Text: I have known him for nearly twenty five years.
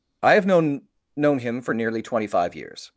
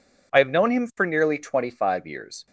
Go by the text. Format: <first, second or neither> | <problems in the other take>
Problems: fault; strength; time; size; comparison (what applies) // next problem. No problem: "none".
second | says "known" twice; at 1.1 s